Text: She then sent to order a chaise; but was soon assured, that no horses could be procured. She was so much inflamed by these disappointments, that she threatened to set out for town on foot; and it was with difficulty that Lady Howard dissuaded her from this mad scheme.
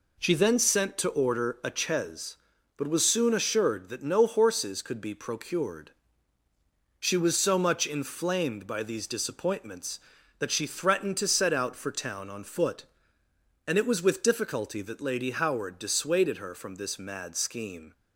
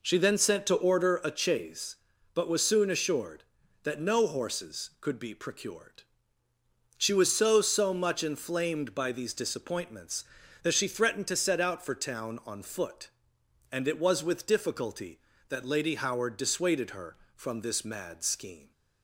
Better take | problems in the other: first | says "so" twice; at 7.6 s

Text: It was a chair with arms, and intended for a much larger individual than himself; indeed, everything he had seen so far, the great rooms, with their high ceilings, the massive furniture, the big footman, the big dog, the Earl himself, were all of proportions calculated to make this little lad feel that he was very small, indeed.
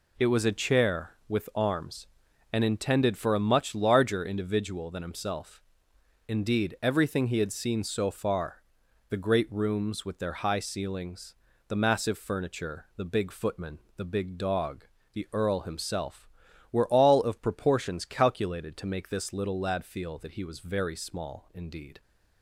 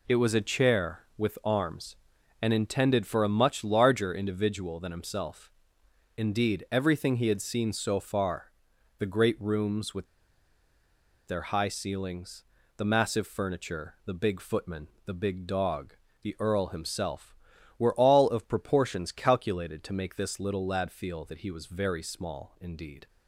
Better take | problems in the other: first | pauses between "with" and "their"; at 10.0 s; 1.2 s long

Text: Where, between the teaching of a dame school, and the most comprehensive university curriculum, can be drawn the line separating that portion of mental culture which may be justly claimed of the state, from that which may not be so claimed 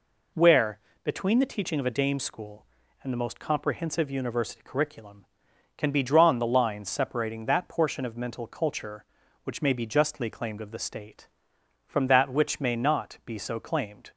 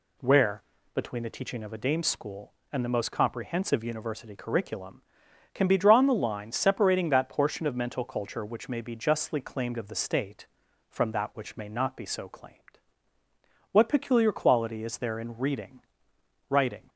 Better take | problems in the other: first | goes on to say "What peculiar quality is there in reading writing"; strong; from 13.7 s on; 3.1 s long

